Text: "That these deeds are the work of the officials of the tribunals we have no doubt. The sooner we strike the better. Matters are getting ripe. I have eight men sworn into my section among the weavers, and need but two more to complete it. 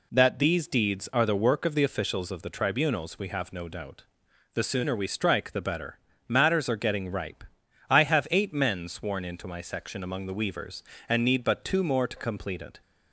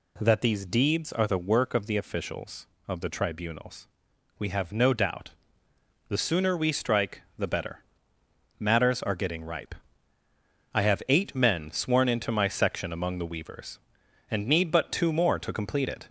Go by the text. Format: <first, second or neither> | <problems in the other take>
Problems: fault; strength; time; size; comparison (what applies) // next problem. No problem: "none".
first | gets louder; slight; throughout; 2.5 dB // pauses between "tribunals" and "we"; noticeable; at 3.8 s; 0.52 s long // pauses between "strike" and "the"; slight; at 7.2 s; 0.16 s long